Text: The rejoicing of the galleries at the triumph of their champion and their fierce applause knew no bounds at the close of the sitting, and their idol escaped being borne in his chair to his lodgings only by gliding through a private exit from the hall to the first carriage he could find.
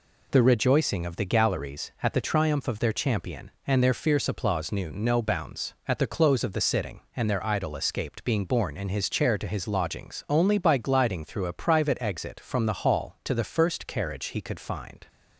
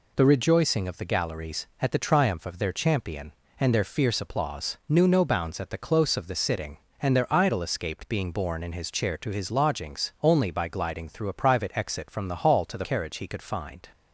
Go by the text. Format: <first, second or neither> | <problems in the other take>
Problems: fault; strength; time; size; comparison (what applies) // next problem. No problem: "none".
first | skips "first"; at 12.8 s